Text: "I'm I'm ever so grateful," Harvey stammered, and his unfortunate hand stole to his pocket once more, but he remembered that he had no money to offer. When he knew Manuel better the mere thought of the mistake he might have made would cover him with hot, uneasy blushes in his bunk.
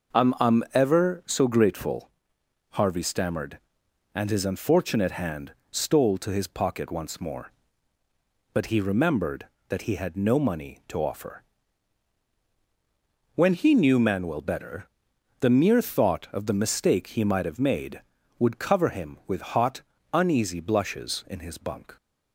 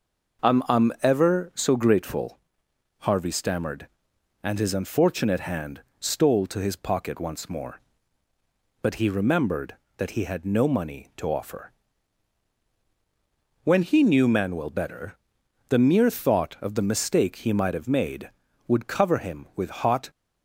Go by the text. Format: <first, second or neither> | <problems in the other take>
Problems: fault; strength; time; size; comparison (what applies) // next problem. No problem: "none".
first | pauses between "hand" and "stole"; slight; at 5.8 s; 0.18 s long; slight in the first // pauses between "better" and "the"; noticeable; at 15.1 s; 0.50 s long; noticeable in the first // stops before "uneasy blushes in his bunk"; at 20.1 s